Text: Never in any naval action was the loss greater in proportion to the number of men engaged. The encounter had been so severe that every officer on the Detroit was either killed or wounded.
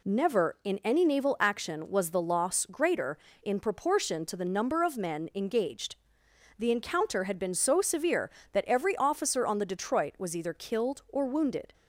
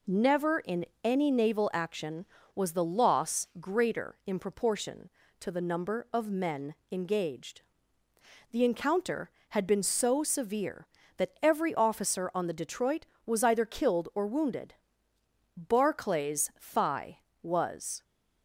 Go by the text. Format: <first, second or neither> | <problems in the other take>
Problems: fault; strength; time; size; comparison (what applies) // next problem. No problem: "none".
first | pauses between "in" and "any"; slight; at 0.8 s; 0.20 s long // pauses between "men" and "engaged"; slight; at 6.7 s; 0.16 s long // goes on to say "Barclay's thigh was"; strong; from 15.5 s on; 2.4 s long